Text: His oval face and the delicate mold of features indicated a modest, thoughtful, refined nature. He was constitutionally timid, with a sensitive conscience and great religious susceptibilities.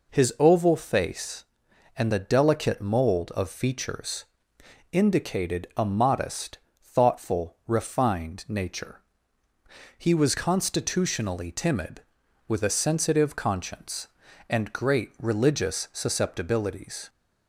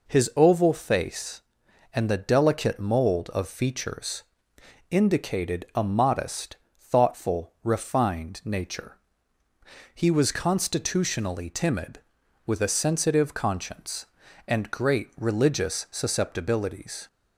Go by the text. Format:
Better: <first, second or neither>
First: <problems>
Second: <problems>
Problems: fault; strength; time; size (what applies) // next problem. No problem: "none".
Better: neither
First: pauses between "features" and "indicated"; noticeable; at 4.2 s; 0.66 s long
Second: pauses between "features" and "indicated"; noticeable; at 4.2 s; 0.66 s long